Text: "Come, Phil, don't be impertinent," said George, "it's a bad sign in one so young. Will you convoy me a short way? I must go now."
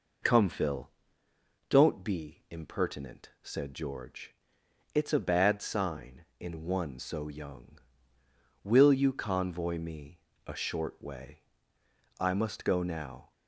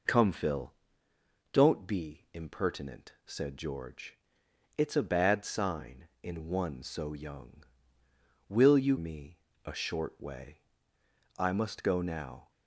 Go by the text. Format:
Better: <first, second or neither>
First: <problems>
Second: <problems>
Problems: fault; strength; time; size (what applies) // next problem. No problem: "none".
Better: first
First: pauses between "me" and "a"; slight; at 10.1 s; 0.26 s long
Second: skips "convoy"; at 8.9 s // pauses between "me" and "a"; slight; at 9.3 s; 0.26 s long